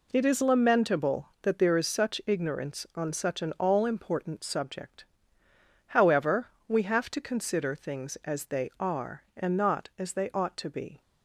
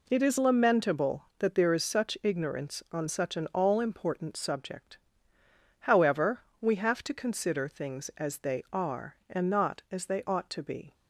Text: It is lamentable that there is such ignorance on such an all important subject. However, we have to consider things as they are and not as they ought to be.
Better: neither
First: none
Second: none

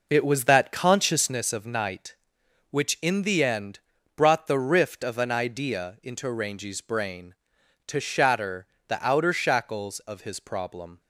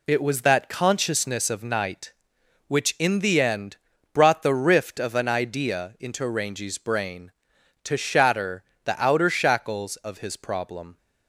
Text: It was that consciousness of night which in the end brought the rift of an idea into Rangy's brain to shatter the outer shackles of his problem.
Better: second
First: starts louder than the rest; noticeable; until 1.4 s; 5 dB // pauses between "end" and "brought"; at 3.7 s; 0.38 s long // pauses between "shatter" and "the"; slight; at 8.6 s; 0.22 s long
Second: pauses between "end" and "brought"; at 3.7 s; 0.38 s long // pauses between "shatter" and "the"; slight; at 8.6 s; 0.22 s long

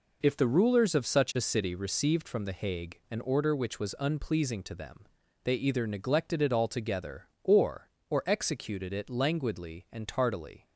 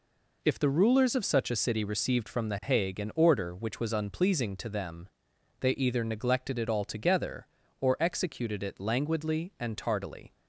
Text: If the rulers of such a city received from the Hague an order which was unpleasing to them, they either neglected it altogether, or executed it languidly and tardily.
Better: second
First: says "or" twice; at 8.0 s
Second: none

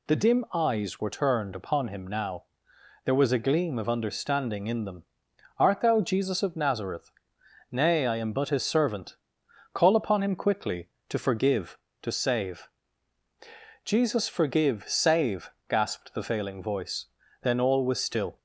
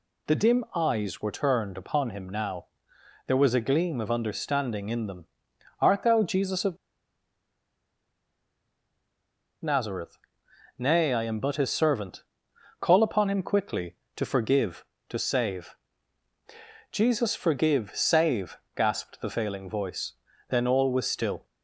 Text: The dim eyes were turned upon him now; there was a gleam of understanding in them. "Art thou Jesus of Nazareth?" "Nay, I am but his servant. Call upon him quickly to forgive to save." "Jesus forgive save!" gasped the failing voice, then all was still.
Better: first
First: none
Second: pauses between "of" and "Nazareth"; strong; at 6.7 s; 2.8 s long

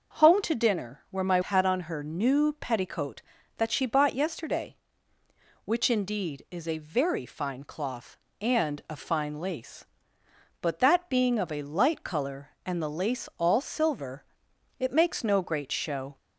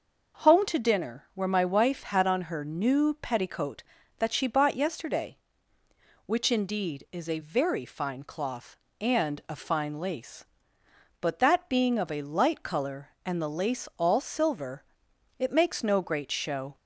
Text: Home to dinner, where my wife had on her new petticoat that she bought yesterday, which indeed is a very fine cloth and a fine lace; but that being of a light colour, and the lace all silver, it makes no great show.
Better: second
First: skips "wife"; at 1.4 s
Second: none

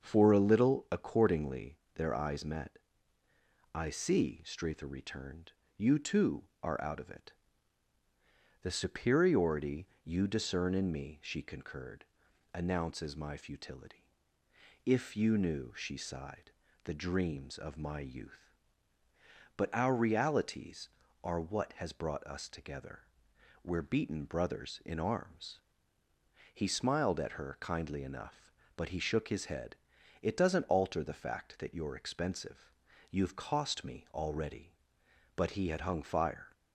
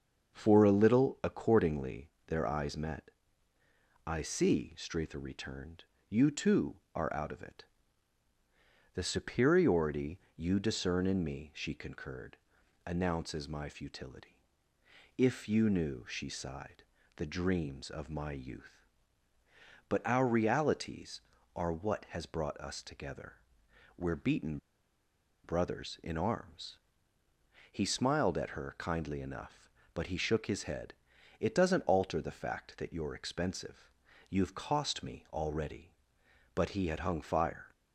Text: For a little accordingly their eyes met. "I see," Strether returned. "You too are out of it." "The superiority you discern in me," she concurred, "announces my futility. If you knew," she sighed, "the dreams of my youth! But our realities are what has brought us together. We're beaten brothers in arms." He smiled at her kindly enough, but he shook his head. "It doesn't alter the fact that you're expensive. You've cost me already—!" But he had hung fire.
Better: first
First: starts louder than the rest; until 1.0 s; 6.5 dB // pauses between "accordingly" and "their"; slight; at 1.7 s; 0.16 s long // pauses between "superiority" and "you"; slight; at 9.8 s; 0.18 s long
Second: starts louder than the rest; until 1.3 s; 6.5 dB // pauses between "accordingly" and "their"; slight; at 2.1 s; 0.16 s long // pauses between "superiority" and "you"; slight; at 10.1 s; 0.18 s long // pauses between "beaten" and "brothers"; noticeable; at 24.5 s; 0.85 s long

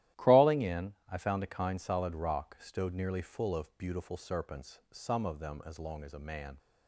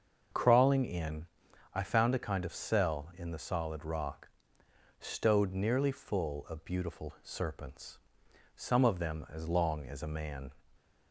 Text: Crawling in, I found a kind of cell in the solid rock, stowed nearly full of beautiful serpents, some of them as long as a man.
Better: second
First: starts louder than the rest; strong; until 1.3 s; 13.5 dB // skips "of cell in the"; at 1.7 s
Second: starts louder than the rest; until 1.8 s; 6.5 dB

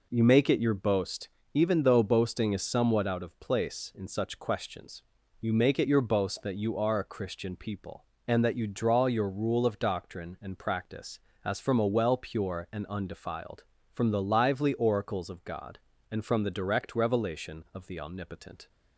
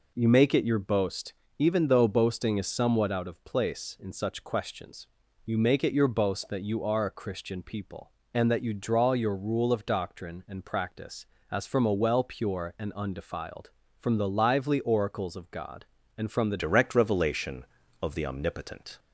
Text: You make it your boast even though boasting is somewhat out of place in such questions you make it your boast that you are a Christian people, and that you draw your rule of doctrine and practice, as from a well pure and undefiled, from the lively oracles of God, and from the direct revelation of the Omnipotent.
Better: first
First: pauses between "boast" and "even"; slight; at 1.2 s; 0.28 s long // pauses between "questions" and "you"; at 5.0 s; 0.38 s long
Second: pauses between "boast" and "even"; slight; at 1.3 s; 0.28 s long // pauses between "questions" and "you"; at 5.0 s; 0.38 s long // changes voice at "direct"; from 16.5 s on; 2.4 s long

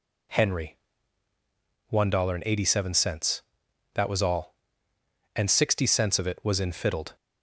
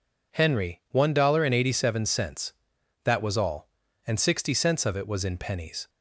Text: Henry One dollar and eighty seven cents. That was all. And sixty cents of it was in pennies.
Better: second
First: pauses between "Henry" and "One"; at 0.7 s; 1.1 s long // says "fiddled" for "pennies"; at 6.7 s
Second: none

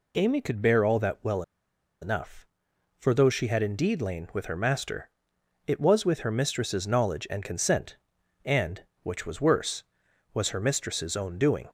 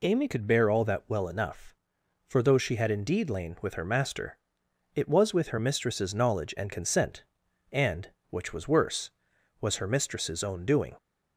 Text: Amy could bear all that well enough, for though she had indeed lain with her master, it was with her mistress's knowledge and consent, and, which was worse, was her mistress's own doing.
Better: second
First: pauses between "well" and "enough"; noticeable; at 1.4 s; 0.59 s long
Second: none

